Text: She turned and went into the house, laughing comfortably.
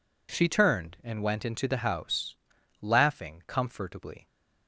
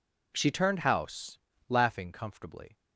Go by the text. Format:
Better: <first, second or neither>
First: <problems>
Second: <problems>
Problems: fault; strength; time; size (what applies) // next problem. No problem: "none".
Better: first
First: none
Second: skips "and went into the"; at 0.7 s